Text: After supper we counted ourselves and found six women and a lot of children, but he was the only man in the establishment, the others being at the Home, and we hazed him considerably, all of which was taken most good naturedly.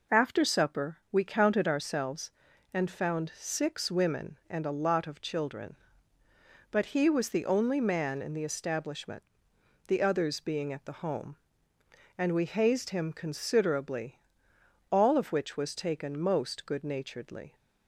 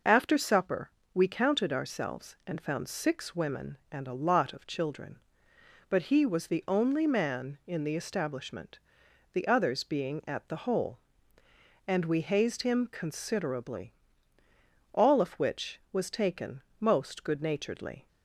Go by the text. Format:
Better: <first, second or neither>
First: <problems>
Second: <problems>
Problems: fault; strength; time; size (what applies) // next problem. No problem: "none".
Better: first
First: pauses between "supper" and "we"; slight; at 0.9 s; 0.16 s long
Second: pauses between "supper" and "we"; slight; at 0.8 s; 0.24 s long // says "Hole" for "Home"; at 10.6 s // pauses between "taken" and "most"; slight; at 16.6 s; 0.16 s long